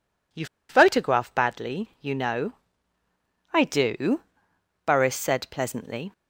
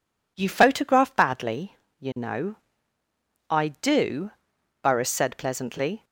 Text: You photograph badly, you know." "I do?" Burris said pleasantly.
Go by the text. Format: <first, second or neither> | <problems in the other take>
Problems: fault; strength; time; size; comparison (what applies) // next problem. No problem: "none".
second | pauses between "You" and "photograph"; slight; at 0.4 s; 0.24 s long